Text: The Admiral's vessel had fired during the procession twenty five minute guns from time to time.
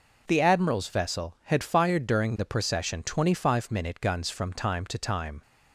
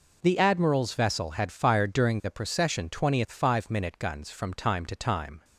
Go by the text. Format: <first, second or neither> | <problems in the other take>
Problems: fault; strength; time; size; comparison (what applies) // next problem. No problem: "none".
first | says "twentieth" for "twenty"; at 2.8 s